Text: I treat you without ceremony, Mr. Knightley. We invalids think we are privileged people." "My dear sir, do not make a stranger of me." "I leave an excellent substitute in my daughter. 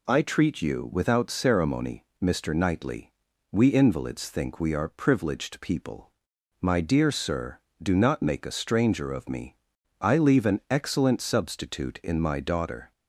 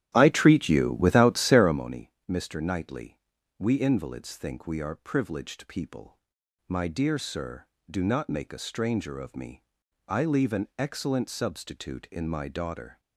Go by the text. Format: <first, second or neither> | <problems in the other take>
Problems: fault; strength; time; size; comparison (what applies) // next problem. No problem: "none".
first | starts louder than the rest; strong; until 1.8 s; 12.5 dB